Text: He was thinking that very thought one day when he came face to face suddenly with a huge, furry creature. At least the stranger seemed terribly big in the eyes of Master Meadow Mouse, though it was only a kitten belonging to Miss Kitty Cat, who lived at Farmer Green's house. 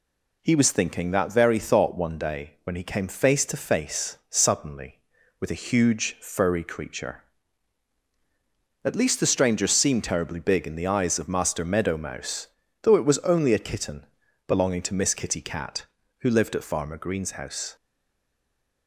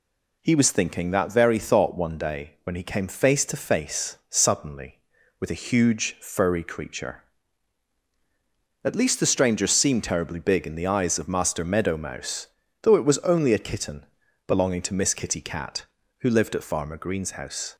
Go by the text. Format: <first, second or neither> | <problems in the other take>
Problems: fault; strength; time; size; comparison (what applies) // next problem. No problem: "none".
second | pauses between "kitten" and "belonging"; at 14.0 s; 0.42 s long; also in the second // stays silent after the last word; from 17.7 s on; 1.1 s long